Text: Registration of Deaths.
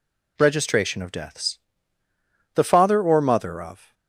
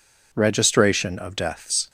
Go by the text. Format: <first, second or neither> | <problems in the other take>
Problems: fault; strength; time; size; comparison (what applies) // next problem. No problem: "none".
second | goes on to say "The father or mother of"; from 2.5 s on; 1.3 s long